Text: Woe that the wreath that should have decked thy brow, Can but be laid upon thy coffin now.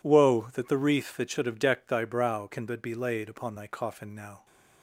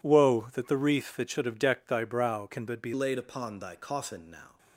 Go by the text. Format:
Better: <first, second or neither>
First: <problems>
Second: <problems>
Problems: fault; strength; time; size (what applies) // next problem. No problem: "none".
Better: first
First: none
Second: changes voice at "laid"; from 2.9 s on; 1.6 s long